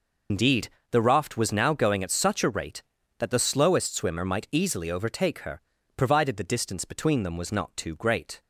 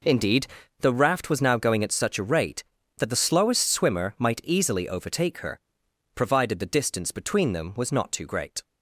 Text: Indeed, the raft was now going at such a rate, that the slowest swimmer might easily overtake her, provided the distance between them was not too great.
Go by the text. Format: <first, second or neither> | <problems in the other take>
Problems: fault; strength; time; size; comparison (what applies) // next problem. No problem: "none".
second | loses the start of "Indeed"; at 0.2 s; 90 ms